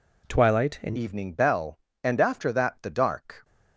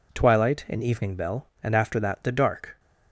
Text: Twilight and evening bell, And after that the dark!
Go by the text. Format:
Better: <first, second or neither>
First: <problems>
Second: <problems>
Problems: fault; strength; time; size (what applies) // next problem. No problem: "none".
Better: second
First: changes voice at "evening"; from 0.9 s on; 2.5 s long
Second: none